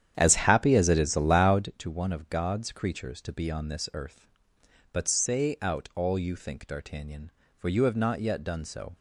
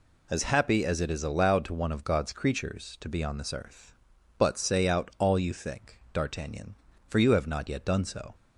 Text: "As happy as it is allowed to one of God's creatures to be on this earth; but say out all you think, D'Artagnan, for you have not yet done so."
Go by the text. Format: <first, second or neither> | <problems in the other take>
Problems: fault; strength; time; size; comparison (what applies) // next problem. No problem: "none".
second | starts louder than the rest; strong; until 1.7 s; 9.5 dB